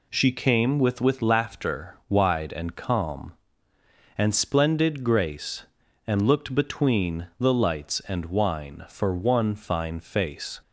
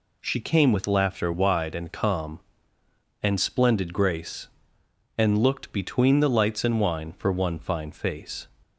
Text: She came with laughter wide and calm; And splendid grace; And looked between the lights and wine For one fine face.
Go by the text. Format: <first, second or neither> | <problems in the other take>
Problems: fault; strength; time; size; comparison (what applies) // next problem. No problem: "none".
second | says "with" twice; at 0.9 s